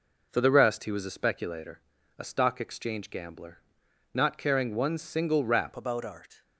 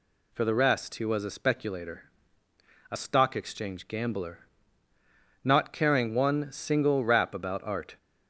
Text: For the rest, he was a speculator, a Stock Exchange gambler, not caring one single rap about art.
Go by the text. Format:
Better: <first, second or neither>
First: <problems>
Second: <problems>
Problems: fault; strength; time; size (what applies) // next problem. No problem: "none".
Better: second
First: changes voice at "about"; from 5.7 s on; 0.7 s long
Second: none